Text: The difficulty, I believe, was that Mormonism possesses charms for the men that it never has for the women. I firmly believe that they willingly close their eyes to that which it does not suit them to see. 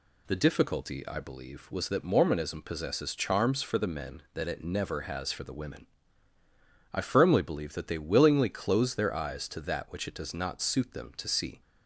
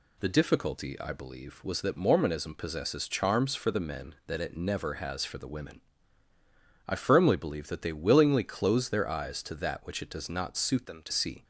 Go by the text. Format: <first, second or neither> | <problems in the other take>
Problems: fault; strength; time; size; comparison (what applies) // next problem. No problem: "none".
first | changes voice from "them" to "to"; from 10.8 to 11.1 s; 0.3 s long